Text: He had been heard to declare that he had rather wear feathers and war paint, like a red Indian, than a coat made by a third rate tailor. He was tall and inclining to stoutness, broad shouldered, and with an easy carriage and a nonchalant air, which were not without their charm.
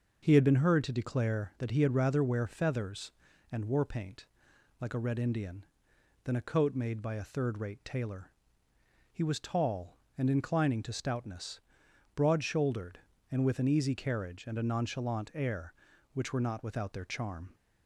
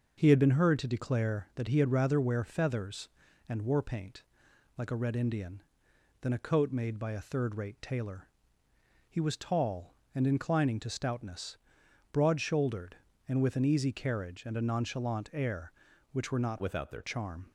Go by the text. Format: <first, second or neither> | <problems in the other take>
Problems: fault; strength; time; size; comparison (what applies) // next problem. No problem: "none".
first | changes voice from "without" to "their"; from 16.6 to 17.0 s; 0.4 s long